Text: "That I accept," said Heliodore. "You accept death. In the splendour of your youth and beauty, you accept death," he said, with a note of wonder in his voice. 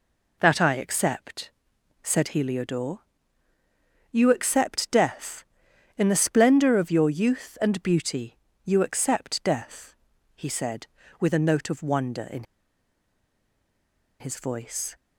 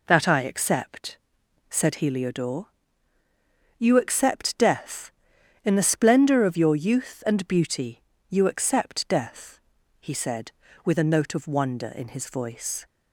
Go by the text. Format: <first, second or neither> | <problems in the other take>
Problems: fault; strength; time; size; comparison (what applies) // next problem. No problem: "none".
second | pauses between "in" and "his"; strong; at 12.4 s; 1.7 s long